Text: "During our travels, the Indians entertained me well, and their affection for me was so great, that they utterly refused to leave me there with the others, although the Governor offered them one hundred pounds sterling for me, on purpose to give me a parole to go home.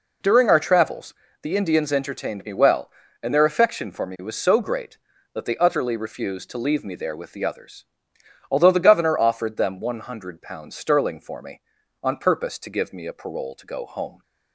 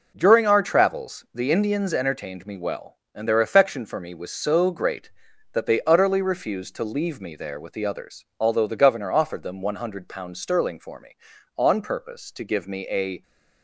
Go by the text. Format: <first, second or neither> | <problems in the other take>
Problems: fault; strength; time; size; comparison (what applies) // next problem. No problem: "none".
first | stops before "parole to go home"; at 13.2 s